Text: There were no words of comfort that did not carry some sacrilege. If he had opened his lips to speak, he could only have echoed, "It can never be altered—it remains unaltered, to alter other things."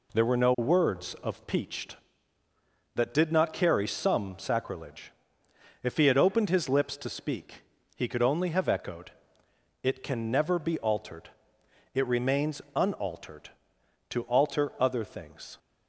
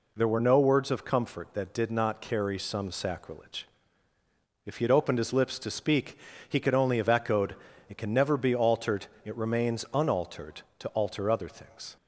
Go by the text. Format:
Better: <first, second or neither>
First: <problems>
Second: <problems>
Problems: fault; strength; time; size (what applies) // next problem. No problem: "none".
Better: second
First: says "peached" for "comfort"; at 1.4 s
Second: none